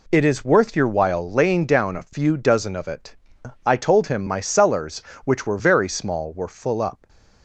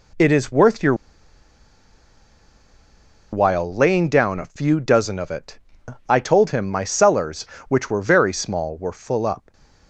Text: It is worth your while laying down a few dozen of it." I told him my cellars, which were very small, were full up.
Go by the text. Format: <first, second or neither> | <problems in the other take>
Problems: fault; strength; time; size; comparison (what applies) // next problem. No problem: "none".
first | pauses between "your" and "while"; strong; at 0.9 s; 2.3 s long // stays silent after the last word; slight; from 9.3 s on; 0.5 s long; slight in the first